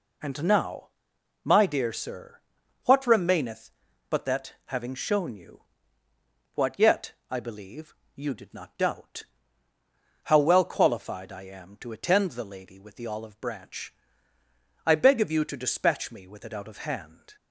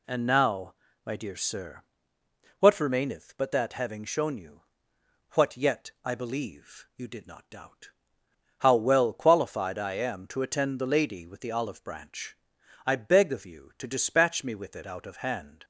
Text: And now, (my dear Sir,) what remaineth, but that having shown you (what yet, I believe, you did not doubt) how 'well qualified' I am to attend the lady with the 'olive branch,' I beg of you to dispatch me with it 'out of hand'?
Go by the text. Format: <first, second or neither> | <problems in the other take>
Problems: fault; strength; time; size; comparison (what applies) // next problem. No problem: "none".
neither | none